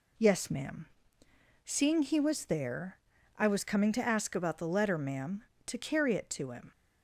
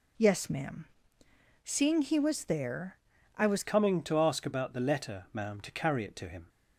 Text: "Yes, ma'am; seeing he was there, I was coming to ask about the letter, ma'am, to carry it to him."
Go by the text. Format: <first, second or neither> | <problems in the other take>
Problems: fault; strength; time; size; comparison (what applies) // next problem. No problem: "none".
first | changes voice at "coming"; from 3.6 s on; 2.8 s long